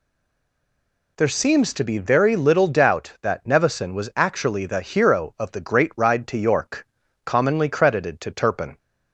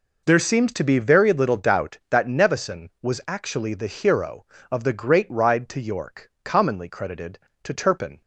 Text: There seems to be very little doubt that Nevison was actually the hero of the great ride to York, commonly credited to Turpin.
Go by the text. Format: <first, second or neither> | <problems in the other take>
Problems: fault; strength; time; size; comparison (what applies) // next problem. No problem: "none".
second | stays silent before the first word; until 1.1 s; 1.1 s long